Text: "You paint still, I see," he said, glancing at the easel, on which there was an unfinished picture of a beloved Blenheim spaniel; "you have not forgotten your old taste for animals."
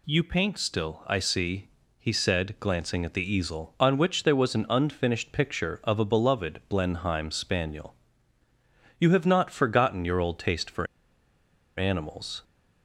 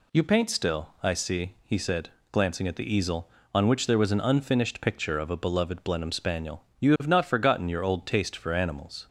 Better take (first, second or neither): second